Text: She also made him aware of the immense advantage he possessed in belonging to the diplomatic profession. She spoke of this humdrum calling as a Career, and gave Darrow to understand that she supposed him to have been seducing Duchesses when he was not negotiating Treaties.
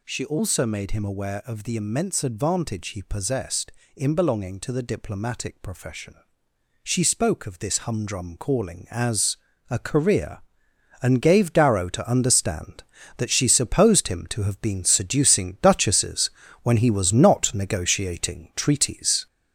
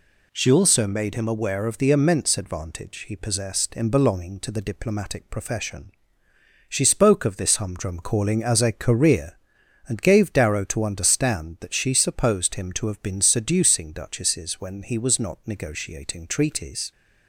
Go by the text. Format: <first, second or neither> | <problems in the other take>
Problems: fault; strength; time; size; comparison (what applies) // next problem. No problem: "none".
second | gets louder; noticeable; throughout; 4.5 dB // pauses between "as" and "a"; slight; at 9.3 s; 0.34 s long // pauses between "Duchesses" and "when"; slight; at 16.3 s; 0.32 s long